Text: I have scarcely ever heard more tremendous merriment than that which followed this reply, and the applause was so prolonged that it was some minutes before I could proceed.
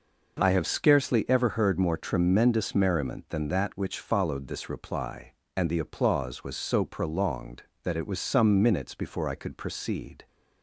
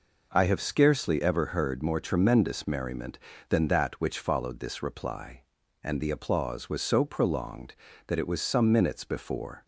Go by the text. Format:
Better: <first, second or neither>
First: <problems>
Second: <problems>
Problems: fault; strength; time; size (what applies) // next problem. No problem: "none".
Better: first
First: none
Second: stops before "I could proceed"; at 9.6 s